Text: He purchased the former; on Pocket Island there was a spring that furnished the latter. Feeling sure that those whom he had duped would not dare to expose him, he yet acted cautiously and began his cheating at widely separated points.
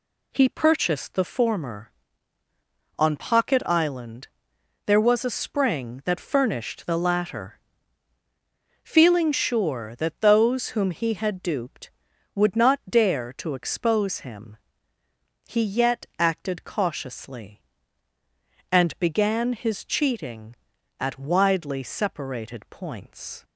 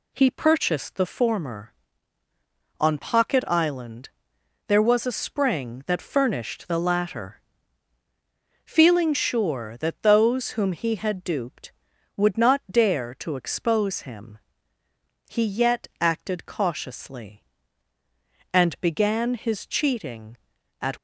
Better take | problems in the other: first | pauses between "Island" and "there"; noticeable; at 4.0 s; 0.58 s long; noticeable in the first // stops before "widely separated points"; at 20.9 s

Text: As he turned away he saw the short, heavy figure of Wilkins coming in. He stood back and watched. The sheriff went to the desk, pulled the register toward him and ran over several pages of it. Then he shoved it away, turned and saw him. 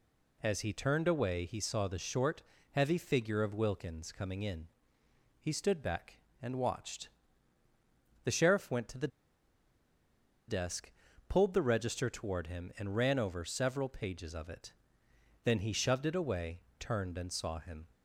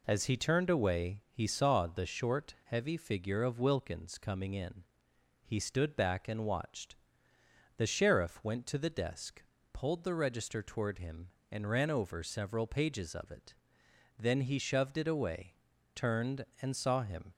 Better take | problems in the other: second | pauses between "the" and "desk"; strong; at 9.0 s; 1.4 s long

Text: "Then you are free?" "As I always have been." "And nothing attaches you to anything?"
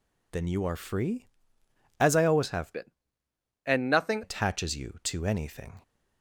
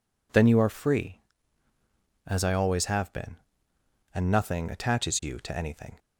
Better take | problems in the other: second | changes voice from "been" to "nothing"; from 2.7 to 4.2 s; 1.5 s long

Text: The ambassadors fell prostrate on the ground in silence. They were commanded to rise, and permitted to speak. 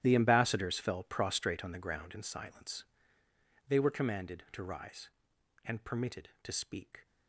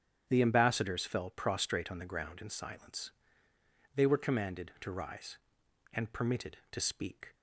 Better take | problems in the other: second | gets quieter; strong; throughout; 16.5 dB // starts louder than the rest; strong; until 1.0 s; 12.5 dB; strong in the second

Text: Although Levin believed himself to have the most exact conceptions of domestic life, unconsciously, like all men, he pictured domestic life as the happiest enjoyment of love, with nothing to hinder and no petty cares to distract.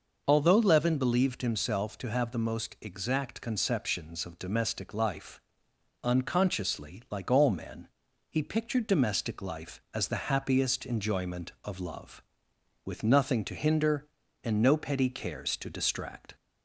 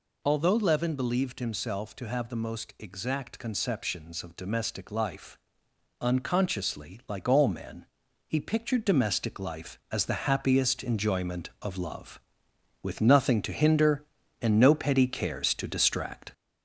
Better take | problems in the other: first | gets louder; noticeable; throughout; 4 dB

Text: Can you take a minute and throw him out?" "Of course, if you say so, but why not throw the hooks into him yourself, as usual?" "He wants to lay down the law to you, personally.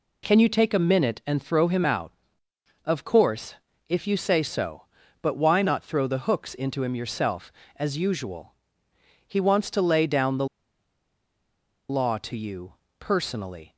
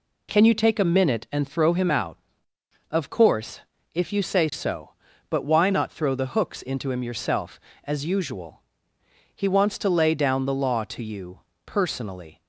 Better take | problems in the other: second | pauses between "the" and "law"; strong; at 10.4 s; 1.4 s long

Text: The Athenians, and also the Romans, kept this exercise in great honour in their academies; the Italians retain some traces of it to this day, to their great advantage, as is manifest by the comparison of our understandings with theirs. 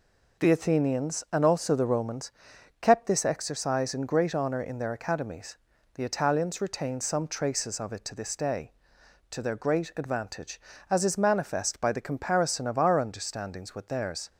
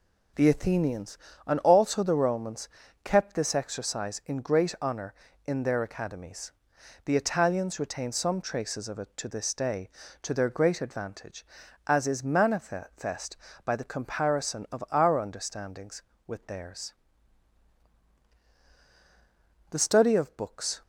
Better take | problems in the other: first | goes on to say "The study of books"; noticeable; from 19.6 s on; 1.1 s long

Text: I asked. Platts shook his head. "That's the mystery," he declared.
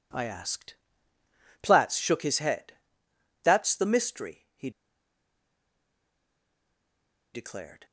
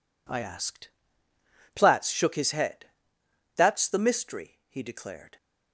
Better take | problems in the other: second | pauses between "he" and "declared"; strong; at 4.6 s; 2.6 s long

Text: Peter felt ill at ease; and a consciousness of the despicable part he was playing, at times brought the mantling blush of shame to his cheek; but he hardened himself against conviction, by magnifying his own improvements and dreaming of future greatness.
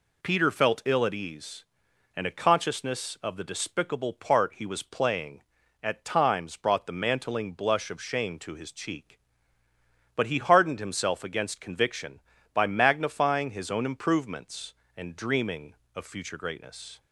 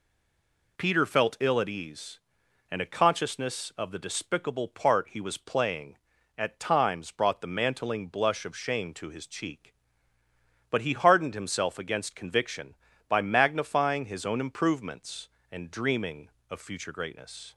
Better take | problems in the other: first | stays silent before the first word; slight; until 0.7 s; 0.7 s long

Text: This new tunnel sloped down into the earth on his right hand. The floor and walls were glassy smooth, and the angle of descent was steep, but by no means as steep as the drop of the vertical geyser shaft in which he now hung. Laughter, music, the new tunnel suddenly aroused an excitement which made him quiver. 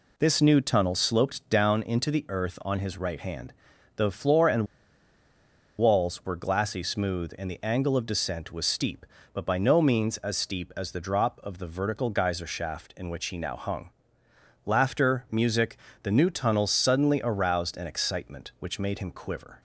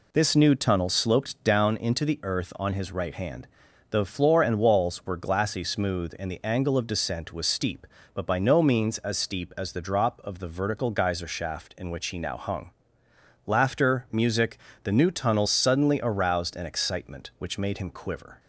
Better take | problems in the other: second | pauses between "and" and "walls"; at 4.6 s; 1.1 s long

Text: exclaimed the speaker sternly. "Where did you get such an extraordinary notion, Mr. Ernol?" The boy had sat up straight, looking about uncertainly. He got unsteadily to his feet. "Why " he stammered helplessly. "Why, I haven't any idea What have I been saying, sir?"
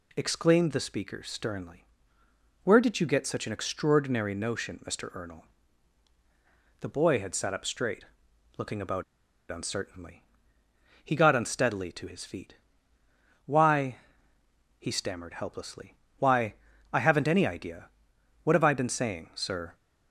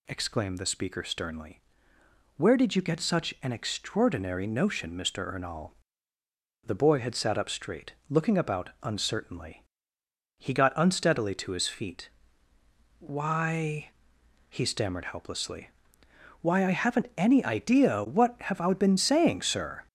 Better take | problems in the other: second | pauses between "about" and "uncertainly"; noticeable; at 9.0 s; 0.47 s long // pauses between "idea" and "What"; noticeable; at 17.8 s; 0.54 s long

